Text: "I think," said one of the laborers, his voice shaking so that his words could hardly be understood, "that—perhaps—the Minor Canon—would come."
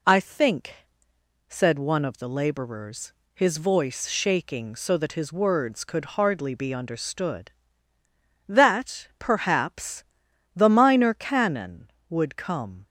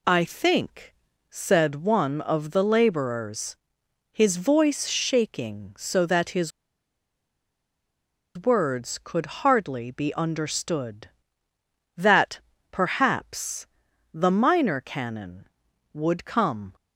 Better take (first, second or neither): first